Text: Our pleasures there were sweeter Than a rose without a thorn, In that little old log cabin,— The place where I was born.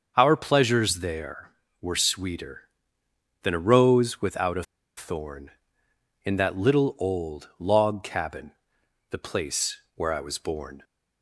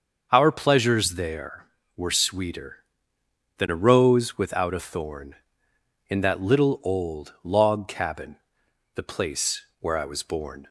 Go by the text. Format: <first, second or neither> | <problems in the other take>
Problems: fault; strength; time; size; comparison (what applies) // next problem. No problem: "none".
second | starts louder than the rest; until 1.1 s; 6.5 dB; also in the second // pauses between "a" and "thorn"; slight; at 4.6 s; 0.33 s long // pauses between "place" and "where"; slight; at 9.7 s; 0.18 s long; slight in the second